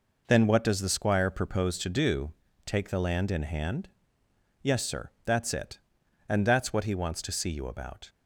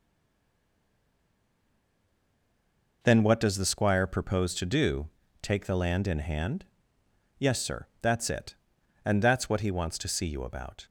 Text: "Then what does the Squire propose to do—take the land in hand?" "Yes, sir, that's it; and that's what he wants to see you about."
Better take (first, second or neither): first